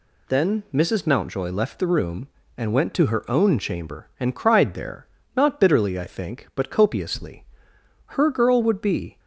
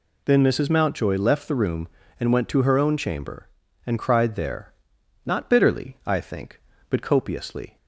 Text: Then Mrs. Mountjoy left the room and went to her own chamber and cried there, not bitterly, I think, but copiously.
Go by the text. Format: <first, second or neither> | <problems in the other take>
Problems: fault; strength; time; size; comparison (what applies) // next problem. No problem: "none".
second | goes on to say "Her girl would be"; noticeable; from 8.0 s on; 1.1 s long